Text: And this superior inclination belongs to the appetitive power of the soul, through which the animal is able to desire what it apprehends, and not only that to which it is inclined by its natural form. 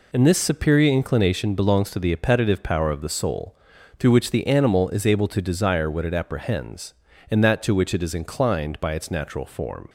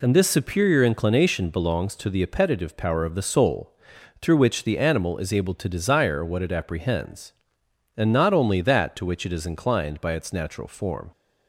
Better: second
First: skips "not only"; at 7.4 s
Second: none

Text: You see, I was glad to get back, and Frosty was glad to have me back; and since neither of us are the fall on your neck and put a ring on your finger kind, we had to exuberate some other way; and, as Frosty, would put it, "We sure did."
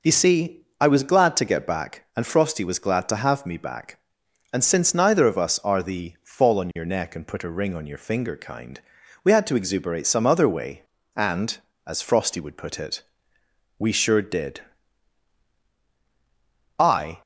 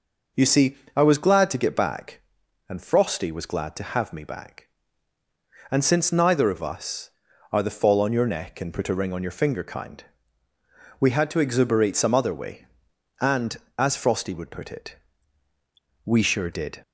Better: second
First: goes on to say "I"; slight; from 16.7 s on; 0.44 s long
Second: none

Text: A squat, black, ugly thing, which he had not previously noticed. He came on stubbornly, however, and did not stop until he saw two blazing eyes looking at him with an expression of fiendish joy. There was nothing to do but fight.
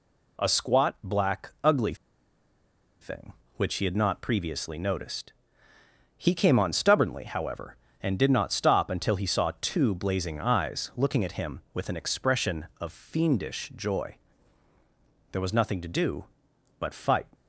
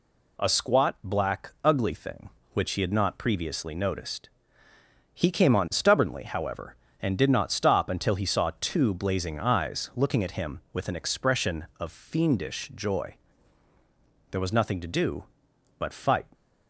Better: second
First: pauses between "ugly" and "thing"; at 1.9 s; 1.0 s long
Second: none

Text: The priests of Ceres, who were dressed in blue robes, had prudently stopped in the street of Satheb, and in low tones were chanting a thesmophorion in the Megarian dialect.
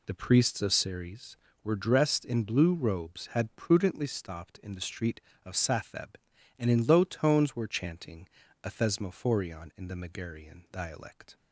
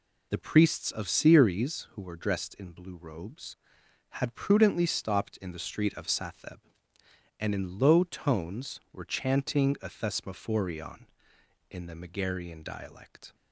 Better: second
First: skips "who"; at 1.4 s // pauses between "chanting" and "a"; slight; at 8.2 s; 0.36 s long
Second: none

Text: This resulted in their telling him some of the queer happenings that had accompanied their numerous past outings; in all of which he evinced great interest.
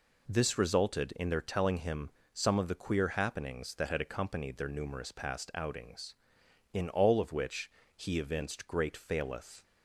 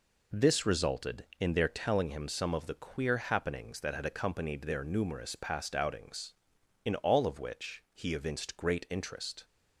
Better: second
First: pauses between "him" and "some"; slight; at 2.1 s; 0.22 s long // pauses between "which" and "he"; slight; at 7.7 s; 0.24 s long // says "faileth" for "interest"; at 8.9 s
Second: none

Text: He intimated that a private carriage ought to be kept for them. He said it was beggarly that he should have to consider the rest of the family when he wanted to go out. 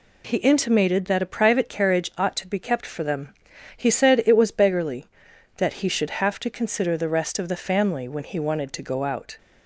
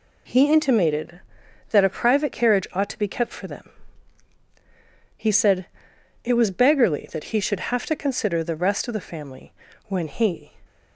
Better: first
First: none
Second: pauses between "said" and "it"; noticeable; at 5.6 s; 0.58 s long // pauses between "family" and "when"; slight; at 9.5 s; 0.34 s long // stops before "wanted to go out"; at 10.6 s

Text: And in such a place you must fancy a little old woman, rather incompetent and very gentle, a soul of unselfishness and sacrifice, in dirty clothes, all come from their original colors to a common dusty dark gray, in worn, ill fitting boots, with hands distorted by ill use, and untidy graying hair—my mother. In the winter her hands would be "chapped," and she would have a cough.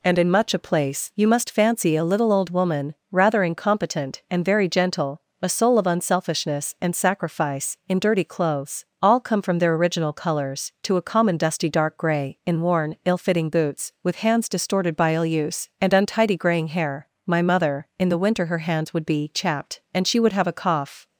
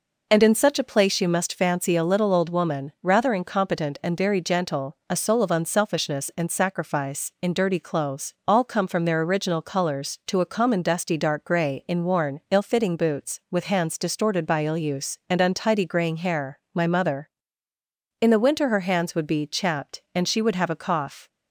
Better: second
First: says "much" for "such"; at 0.3 s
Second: none

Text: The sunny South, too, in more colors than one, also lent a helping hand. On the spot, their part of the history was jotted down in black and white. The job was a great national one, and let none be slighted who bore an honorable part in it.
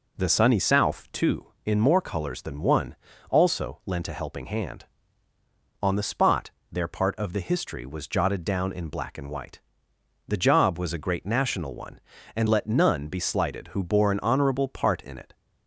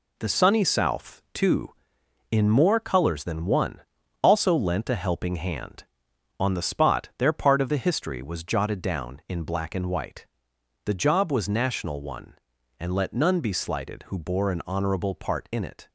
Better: first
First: none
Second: skips "a great"; at 11.4 s

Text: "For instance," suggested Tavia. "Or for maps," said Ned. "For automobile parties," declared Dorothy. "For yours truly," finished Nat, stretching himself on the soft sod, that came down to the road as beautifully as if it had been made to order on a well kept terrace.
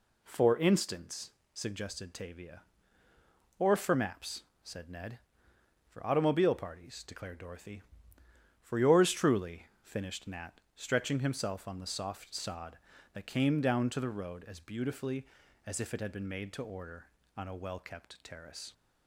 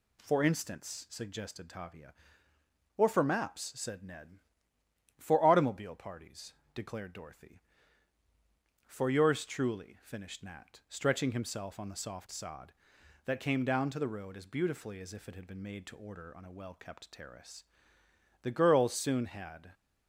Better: first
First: none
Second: goes on to say "The girls soon had"; noticeable; from 18.4 s on; 1.3 s long

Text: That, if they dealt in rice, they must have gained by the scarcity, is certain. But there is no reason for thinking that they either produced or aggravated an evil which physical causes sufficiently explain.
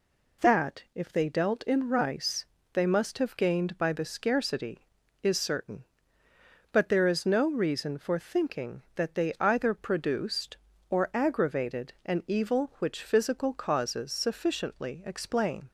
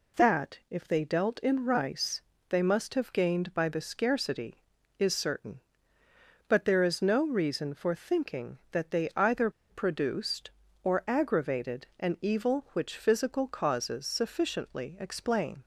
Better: first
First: none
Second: pauses between "either" and "produced"; slight; at 9.4 s; 0.20 s long

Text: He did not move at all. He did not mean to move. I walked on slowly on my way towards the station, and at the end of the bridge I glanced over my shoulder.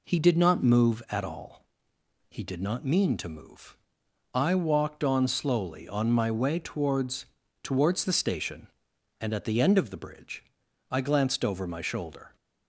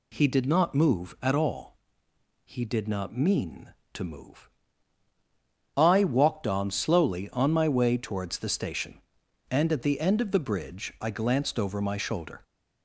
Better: second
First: says "towards" twice; at 7.6 s // pauses between "bridge" and "I"; noticeable; at 10.4 s; 0.48 s long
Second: none

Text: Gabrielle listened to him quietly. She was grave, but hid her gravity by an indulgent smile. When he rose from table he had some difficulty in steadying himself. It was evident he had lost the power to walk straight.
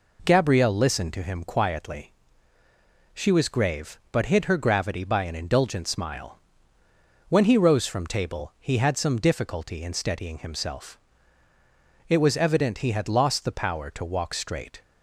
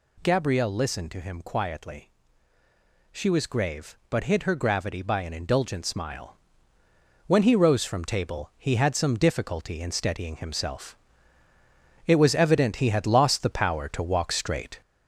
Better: first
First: none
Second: gets louder; noticeable; throughout; 4.5 dB

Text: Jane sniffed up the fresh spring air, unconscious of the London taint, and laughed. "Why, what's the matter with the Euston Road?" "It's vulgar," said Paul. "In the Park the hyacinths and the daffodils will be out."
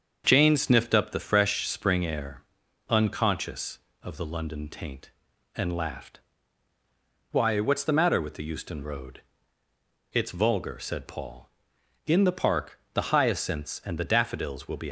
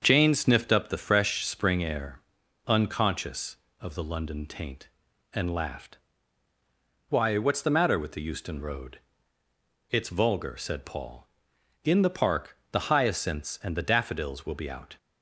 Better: second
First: starts louder than the rest; until 1.2 s; 7 dB // pauses between "Park" and "the"; slight; at 12.7 s; 0.16 s long // stops before "out"; at 14.8 s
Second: starts louder than the rest; until 1.0 s; 7 dB // pauses between "Park" and "the"; slight; at 12.5 s; 0.16 s long

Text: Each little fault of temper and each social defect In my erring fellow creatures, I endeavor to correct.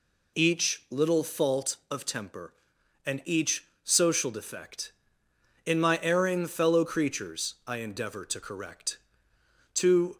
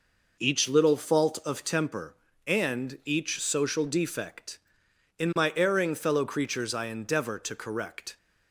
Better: second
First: pauses between "each" and "social"; slight; at 3.6 s; 0.18 s long // goes on to say "To"; slight; from 9.7 s on; 0.42 s long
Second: none

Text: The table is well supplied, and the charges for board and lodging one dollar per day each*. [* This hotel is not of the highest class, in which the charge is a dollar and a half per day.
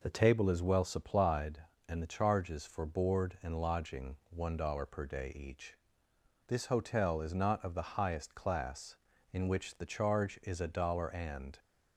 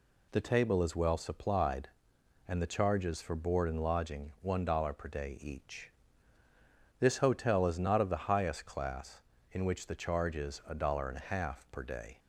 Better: second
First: stops before "a half per day"; at 11.5 s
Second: none

